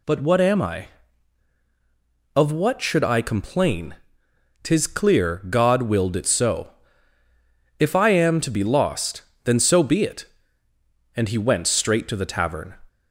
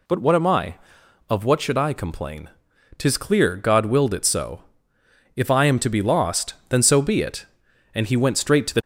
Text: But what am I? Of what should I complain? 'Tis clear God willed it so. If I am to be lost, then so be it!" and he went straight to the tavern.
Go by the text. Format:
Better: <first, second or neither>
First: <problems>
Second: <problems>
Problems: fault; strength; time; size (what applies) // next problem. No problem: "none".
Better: first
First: none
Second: stops before "tavern"; at 8.8 s